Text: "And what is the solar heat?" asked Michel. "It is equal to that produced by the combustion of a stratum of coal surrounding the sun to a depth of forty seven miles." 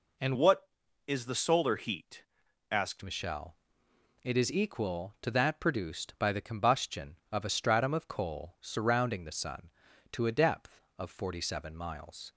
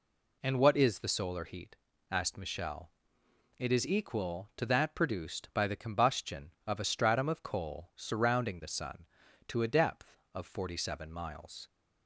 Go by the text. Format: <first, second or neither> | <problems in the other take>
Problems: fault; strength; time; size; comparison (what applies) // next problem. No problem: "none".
second | changes voice from "what" to "asked"; from 0.3 to 3.0 s; 2.7 s long